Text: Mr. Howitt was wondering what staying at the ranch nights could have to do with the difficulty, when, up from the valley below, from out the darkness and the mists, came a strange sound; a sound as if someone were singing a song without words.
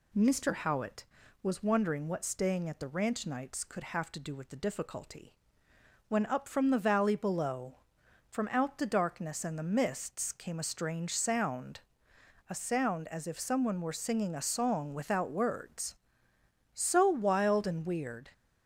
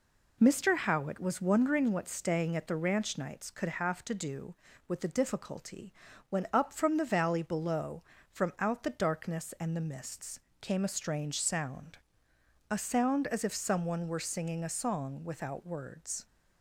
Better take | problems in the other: second | goes on to say "So wild and weird"; from 16.7 s on; 1.5 s long

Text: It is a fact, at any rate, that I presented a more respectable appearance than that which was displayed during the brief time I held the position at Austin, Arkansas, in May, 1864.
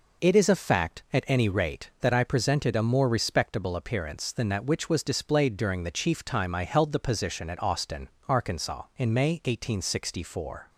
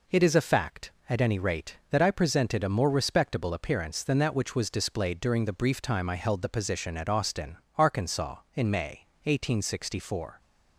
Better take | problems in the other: second | says "chief" for "brief"; at 5.9 s

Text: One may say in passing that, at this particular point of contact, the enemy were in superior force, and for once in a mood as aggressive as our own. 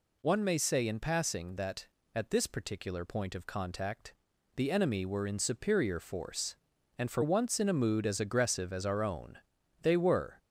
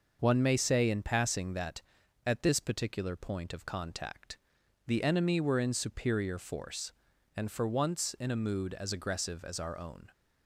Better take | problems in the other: second | goes on to say "They were"; from 9.8 s on; 0.58 s long

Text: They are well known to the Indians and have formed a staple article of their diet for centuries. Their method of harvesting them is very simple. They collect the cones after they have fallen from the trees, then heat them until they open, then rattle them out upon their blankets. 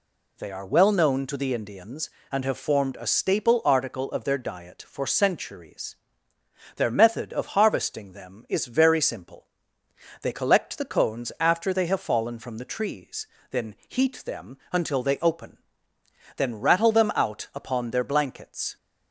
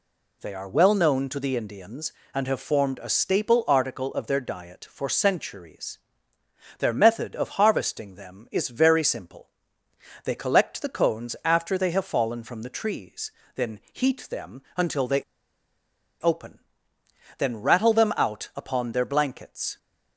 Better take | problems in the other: first | pauses between "them" and "until"; slight; at 14.6 s; 0.16 s long; slight in the first // pauses between "they" and "open"; noticeable; at 15.2 s; 0.97 s long

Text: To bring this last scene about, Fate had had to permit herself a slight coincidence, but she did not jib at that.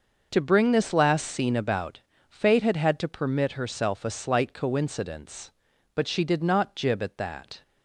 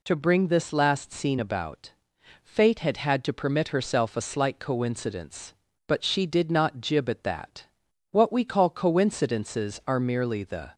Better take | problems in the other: first | goes on to say "What we call coincidences are merely the"; strong; from 8.1 s on; 2.6 s long

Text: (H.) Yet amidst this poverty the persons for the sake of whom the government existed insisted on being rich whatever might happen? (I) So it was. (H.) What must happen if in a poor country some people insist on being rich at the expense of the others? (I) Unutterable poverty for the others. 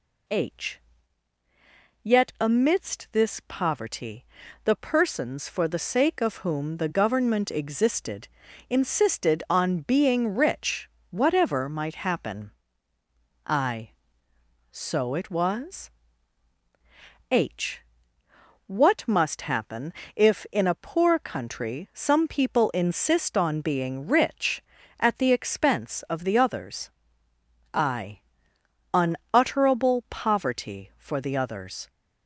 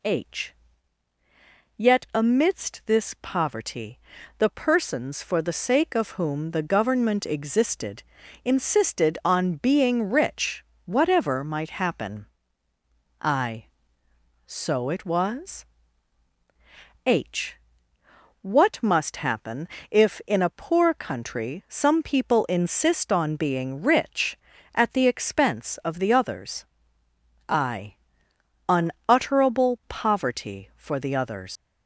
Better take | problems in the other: first | pauses between "poverty" and "the"; at 3.9 s; 0.40 s long; also in the first // pauses between "existed" and "insisted"; at 8.0 s; 0.40 s long; also in the first // pauses between "rich" and "whatever"; slight; at 10.6 s; 0.22 s long; slight in the first // pauses between "happen" and "if"; slight; at 19.6 s; 0.22 s long; slight in the first // leaves "others" unfinished; at 31.5 s; 130 ms

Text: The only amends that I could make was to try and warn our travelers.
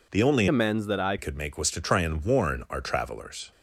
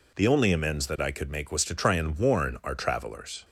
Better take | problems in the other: second | changes voice from "amends" to "I"; from 0.4 to 1.1 s; 0.7 s long

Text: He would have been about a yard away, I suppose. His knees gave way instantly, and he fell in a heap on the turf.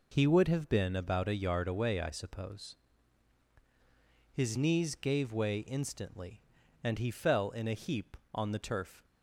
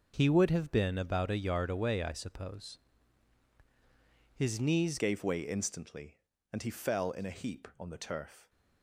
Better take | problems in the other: first | changes voice at "gave"; from 4.9 s on; 3.5 s long

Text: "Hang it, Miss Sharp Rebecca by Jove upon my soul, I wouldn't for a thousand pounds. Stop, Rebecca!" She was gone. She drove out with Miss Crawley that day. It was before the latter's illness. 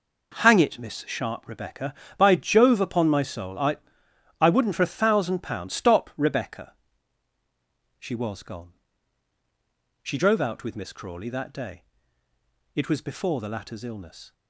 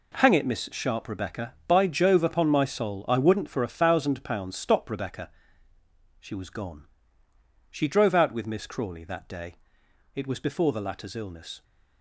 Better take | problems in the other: second | says "I" twice; at 4.4 s

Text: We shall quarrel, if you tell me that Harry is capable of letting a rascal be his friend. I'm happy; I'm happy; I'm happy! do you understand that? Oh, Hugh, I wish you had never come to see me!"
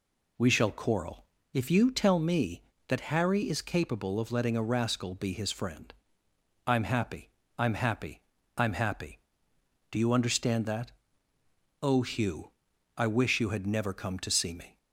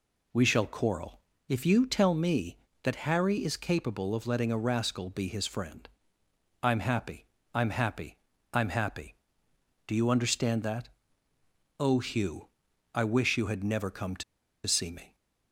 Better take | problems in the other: first | pauses between "to" and "see"; at 14.2 s; 0.43 s long

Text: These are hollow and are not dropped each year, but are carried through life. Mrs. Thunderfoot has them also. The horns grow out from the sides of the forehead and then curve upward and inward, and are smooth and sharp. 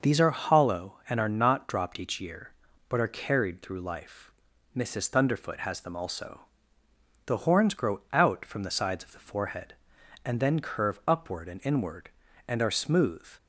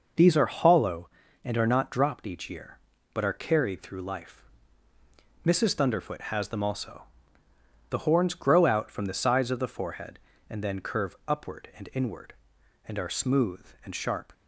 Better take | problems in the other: second | stops before "and sharp"; at 13.3 s

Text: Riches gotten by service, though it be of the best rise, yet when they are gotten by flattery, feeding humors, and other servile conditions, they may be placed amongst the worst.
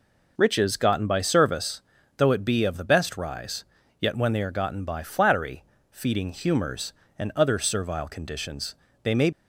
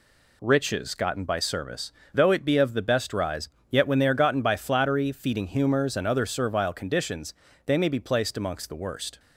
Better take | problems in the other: second | stops before "be placed amongst the worst"; at 9.3 s

